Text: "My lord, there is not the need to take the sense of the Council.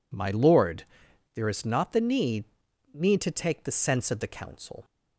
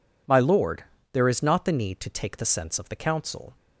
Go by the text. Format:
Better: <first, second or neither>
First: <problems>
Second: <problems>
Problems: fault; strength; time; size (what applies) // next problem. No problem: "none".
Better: second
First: says "need" twice; at 2.9 s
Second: none